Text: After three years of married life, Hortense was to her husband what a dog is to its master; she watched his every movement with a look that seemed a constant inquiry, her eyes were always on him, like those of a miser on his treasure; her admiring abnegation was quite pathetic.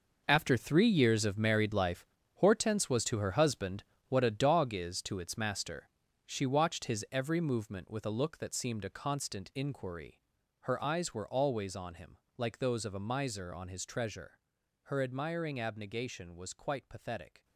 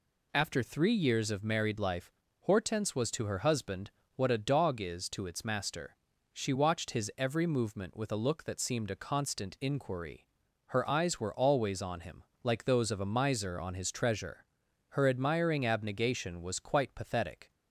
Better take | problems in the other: second | gets quieter; strong; throughout; 13 dB // pauses between "husband" and "what"; slight; at 3.8 s; 0.26 s long; slight in the second

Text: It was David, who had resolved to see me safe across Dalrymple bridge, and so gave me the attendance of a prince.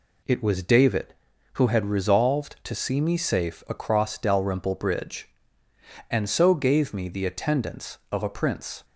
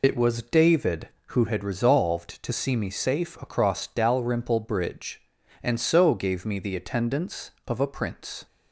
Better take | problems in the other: first | loses the start of "It"; at 0.0 s; 70 ms

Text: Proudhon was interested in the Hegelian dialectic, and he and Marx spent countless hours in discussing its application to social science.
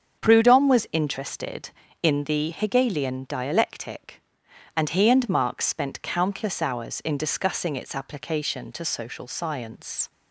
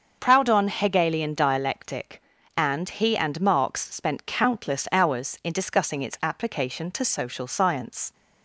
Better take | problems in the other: first | starts louder than the rest; until 1.2 s; 6.5 dB; also in the first // skips "was interested in the"; at 0.6 s

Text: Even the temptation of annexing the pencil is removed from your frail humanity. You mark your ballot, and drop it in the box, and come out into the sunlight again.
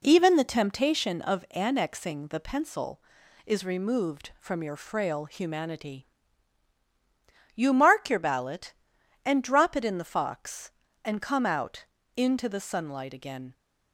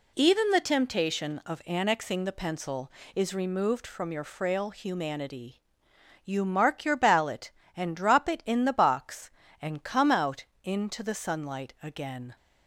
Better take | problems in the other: second | says "fox" for "box"; at 10.1 s // pauses between "out" and "into"; slight; at 11.8 s; 0.32 s long; slight in the second

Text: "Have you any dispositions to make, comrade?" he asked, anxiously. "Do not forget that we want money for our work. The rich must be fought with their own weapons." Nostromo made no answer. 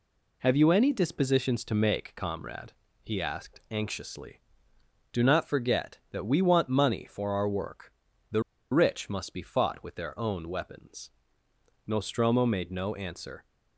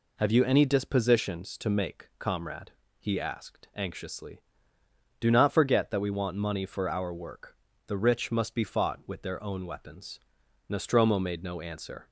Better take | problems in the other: second | pauses between "The" and "rich"; slight; at 8.4 s; 0.30 s long

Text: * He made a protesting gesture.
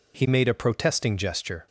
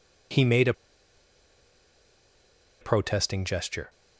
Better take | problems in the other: first | pauses between "a" and "protesting"; strong; at 0.7 s; 2.0 s long

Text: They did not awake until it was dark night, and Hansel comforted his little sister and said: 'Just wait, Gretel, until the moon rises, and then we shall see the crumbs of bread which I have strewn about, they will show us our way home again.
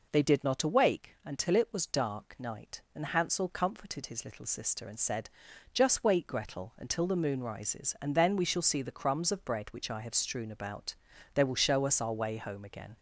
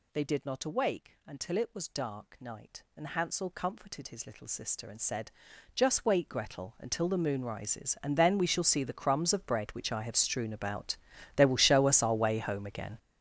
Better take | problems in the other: first | gets louder; strong; throughout; 14.5 dB

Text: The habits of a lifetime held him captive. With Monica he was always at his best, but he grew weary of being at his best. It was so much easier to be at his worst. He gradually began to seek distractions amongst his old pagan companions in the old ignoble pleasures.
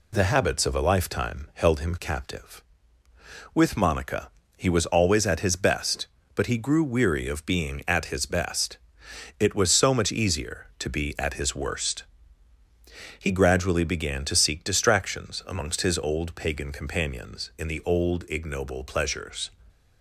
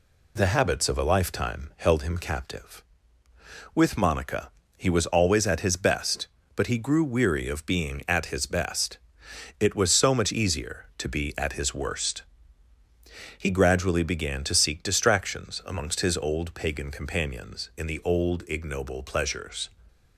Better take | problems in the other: neither | pauses between "Monica" and "he"; slight; the same in both

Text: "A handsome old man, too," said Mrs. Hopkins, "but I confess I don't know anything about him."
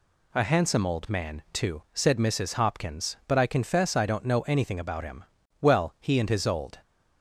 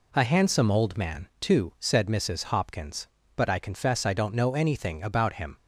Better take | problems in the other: second | goes on to say "Well he and his old"; noticeable; from 5.5 s on; 1.1 s long

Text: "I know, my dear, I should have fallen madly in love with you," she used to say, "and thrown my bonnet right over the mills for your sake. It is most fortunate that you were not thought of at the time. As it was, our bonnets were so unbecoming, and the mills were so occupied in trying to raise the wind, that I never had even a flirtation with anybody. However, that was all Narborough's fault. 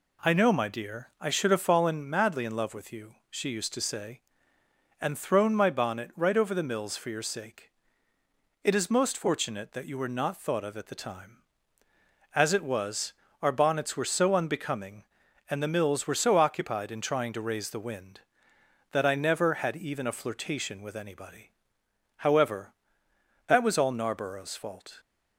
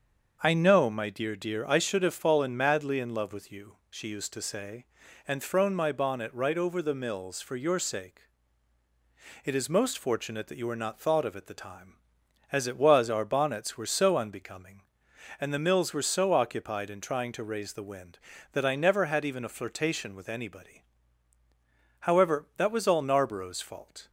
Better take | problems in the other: first | starts louder than the rest; until 1.4 s; 6.5 dB // says "dear" twice; at 1.3 s

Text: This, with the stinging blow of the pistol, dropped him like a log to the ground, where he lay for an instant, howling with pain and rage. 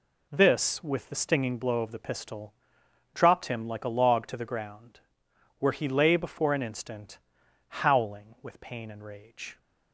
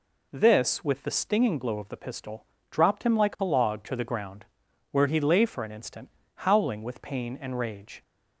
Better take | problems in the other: second | says "before" for "for"; at 6.1 s

